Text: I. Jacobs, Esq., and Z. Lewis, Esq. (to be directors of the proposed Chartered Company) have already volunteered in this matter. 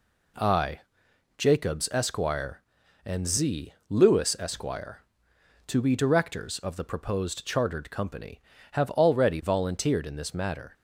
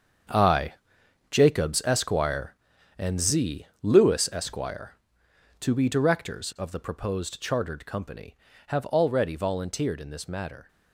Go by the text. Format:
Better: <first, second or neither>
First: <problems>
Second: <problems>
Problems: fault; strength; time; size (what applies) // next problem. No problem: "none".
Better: first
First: none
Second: gets quieter; strong; throughout; 11.5 dB